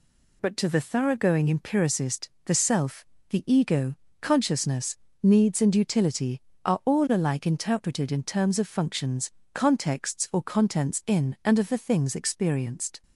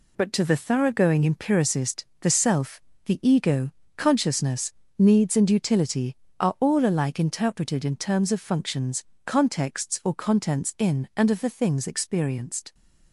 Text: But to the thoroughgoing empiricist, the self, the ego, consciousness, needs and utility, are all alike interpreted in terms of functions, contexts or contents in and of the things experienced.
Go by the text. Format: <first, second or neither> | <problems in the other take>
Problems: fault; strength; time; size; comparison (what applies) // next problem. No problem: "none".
first | gets quieter; throughout; 6.5 dB